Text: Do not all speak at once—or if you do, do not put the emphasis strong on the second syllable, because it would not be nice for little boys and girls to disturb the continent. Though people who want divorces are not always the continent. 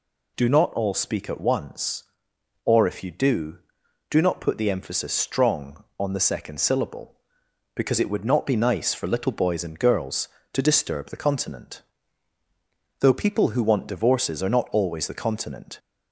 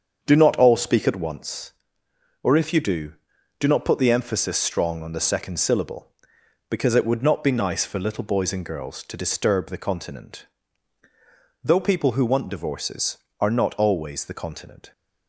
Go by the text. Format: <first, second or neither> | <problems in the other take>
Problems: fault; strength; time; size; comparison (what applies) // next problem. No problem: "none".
first | starts louder than the rest; until 1.3 s; 7 dB